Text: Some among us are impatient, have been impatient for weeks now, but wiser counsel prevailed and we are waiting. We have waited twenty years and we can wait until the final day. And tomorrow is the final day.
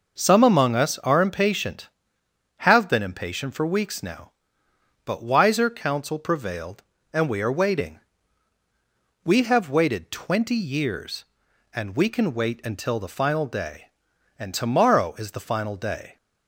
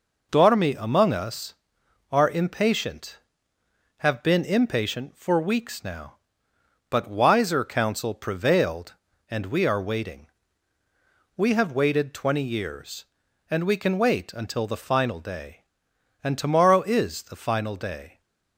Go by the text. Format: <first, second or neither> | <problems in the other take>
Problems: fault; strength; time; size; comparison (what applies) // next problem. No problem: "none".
first | says "Dormi" for "Some"; at 0.3 s